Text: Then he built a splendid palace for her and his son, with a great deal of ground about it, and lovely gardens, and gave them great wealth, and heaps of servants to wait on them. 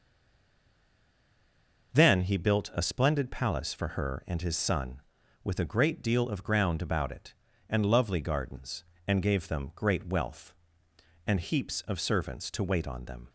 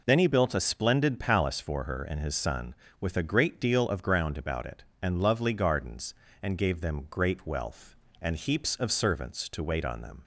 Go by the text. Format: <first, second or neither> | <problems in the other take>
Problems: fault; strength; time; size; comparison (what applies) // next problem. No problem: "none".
second | stays silent before the first word; noticeable; until 1.9 s; 1.9 s long